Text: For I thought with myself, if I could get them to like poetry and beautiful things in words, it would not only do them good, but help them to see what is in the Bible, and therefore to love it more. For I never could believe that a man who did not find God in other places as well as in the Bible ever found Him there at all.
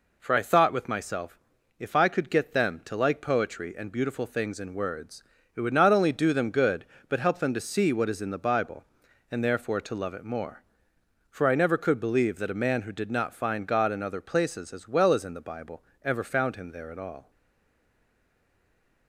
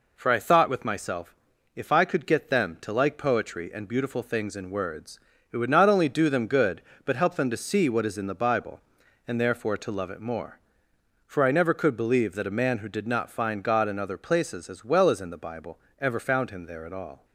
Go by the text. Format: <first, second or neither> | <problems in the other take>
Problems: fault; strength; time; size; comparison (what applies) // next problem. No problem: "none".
second | pauses between "Bible" and "ever"; slight; at 15.8 s; 0.22 s long; slight in the second // stays silent after the last word; noticeable; from 17.3 s on; 1.7 s long